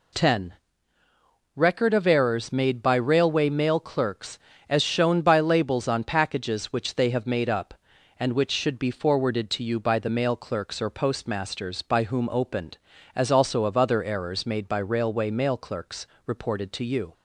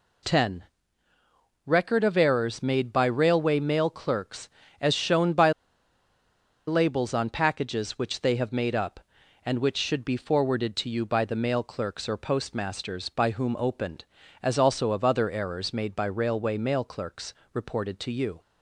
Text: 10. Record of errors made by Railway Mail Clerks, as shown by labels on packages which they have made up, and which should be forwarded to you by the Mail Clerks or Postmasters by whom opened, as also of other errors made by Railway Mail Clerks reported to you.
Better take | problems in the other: first | pauses between "by" and "labels"; at 5.5 s; 1.1 s long // pauses between "Clerks" and "reported"; slight; at 17.3 s; 0.20 s long; slight in the first

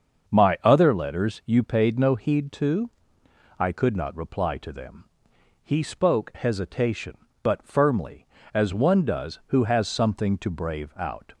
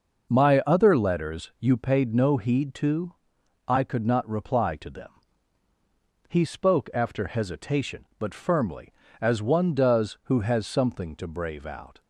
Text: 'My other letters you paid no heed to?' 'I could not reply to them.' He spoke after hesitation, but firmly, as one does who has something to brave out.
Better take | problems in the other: second | starts louder than the rest; until 1.3 s; 6.5 dB // skips "after"; at 6.3 s

